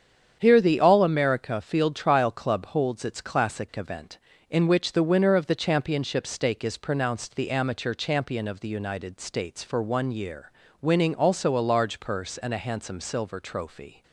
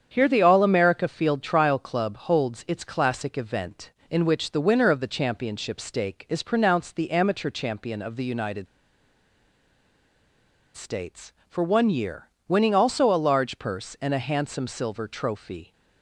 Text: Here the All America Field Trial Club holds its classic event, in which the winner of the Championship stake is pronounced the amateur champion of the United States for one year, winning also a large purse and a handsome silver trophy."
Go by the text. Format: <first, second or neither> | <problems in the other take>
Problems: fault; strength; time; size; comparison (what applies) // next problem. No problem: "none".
first | starts louder than the rest; strong; until 1.1 s; 8 dB; strong in the first // pauses between "United" and "States"; strong; at 8.6 s; 2.0 s long